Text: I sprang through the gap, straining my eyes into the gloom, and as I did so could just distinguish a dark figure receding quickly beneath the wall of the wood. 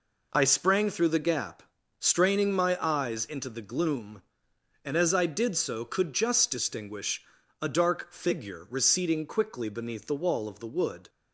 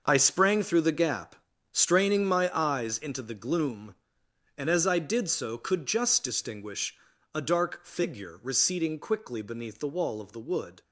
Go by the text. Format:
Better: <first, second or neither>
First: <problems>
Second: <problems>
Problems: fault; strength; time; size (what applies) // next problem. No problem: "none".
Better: first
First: pauses between "distinguish" and "a"; at 7.2 s; 0.38 s long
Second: gets quieter; strong; throughout; 11.5 dB // pauses between "distinguish" and "a"; at 6.9 s; 0.38 s long